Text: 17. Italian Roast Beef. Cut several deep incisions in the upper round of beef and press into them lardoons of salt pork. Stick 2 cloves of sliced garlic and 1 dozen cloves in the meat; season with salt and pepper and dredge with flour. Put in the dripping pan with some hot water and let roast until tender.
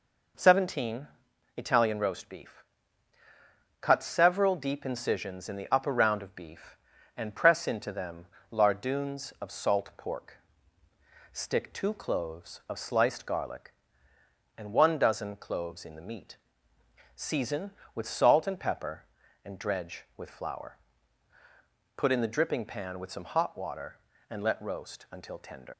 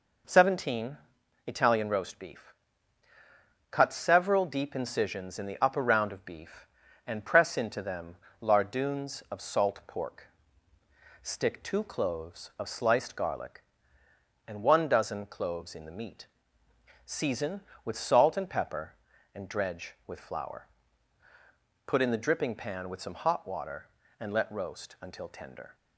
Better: second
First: pauses between "them" and "lardoons"; slight; at 8.2 s; 0.26 s long // leaves "tender" unfinished; at 25.7 s; 110 ms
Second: pauses between "them" and "lardoons"; slight; at 8.1 s; 0.26 s long

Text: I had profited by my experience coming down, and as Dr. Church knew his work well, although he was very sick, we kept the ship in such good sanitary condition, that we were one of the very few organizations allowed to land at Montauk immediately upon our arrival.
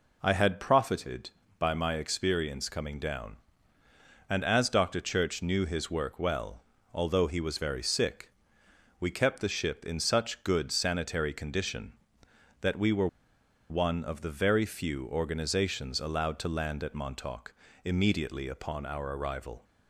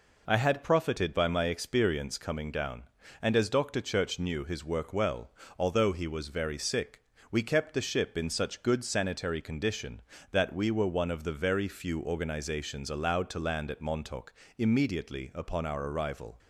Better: second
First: pauses between "were" and "one"; noticeable; at 13.0 s; 0.62 s long // pauses between "Montauk" and "immediately"; slight; at 17.5 s; 0.30 s long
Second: pauses between "Montauk" and "immediately"; slight; at 14.3 s; 0.26 s long

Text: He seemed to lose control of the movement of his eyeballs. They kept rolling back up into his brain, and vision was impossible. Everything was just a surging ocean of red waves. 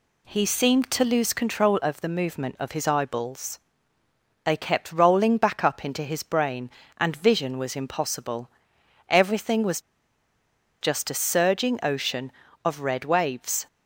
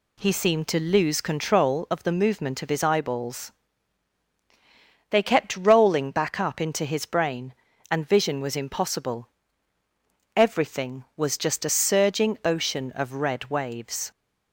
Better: second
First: pauses between "was" and "just"; at 9.7 s; 1.0 s long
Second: none

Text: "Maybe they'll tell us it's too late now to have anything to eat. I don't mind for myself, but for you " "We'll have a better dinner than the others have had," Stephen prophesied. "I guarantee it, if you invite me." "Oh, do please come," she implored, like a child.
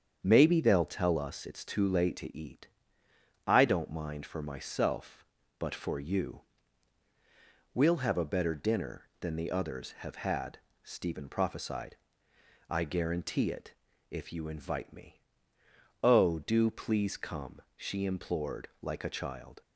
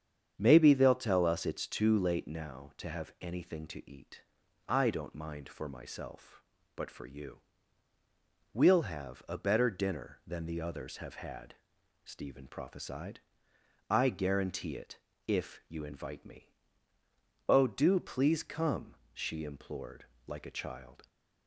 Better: second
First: starts louder than the rest; strong; until 1.2 s; 8 dB // skips "now to have anything"; at 2.1 s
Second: starts louder than the rest; strong; until 1.3 s; 8 dB

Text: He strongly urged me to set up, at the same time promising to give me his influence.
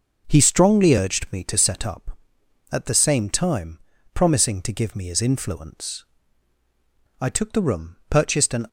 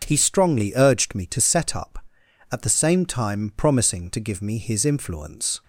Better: second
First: pauses between "time" and "promising"; slight; at 3.7 s; 0.36 s long // goes on to say "I took the room purchased an"; from 7.1 s on; 1.4 s long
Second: none

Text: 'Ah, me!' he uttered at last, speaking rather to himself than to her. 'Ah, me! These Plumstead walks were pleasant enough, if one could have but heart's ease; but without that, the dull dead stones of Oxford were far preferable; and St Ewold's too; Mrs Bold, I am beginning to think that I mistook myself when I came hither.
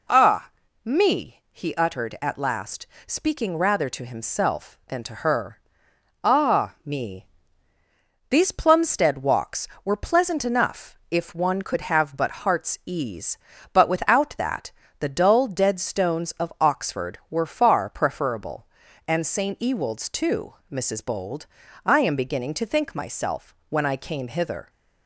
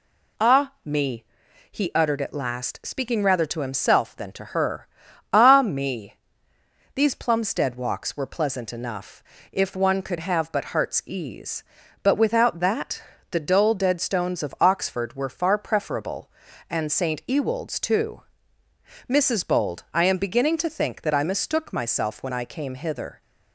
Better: second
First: skips "that I mistook"; at 22.9 s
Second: none

